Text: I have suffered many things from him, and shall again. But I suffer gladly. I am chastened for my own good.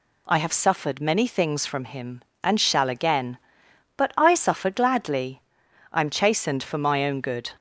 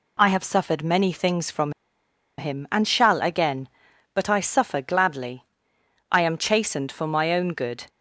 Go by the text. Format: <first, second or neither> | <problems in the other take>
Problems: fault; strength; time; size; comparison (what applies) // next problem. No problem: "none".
first | pauses between "from" and "him"; noticeable; at 1.7 s; 0.67 s long